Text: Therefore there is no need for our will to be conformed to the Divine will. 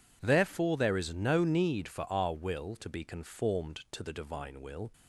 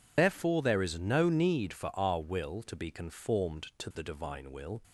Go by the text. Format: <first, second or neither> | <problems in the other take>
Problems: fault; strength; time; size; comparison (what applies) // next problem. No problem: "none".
first | loses the start of "Therefore"; at 0.1 s; 115 ms